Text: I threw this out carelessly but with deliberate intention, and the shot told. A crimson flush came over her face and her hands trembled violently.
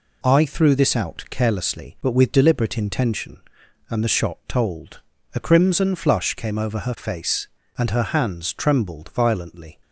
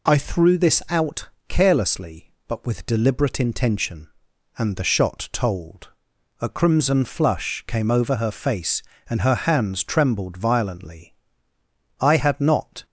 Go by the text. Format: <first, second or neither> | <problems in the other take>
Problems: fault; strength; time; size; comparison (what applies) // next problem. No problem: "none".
first | pauses between "out" and "carelessly"; slight; at 1.2 s; 0.22 s long // goes on to say "I had not"; noticeable; from 11.9 s on; 0.86 s long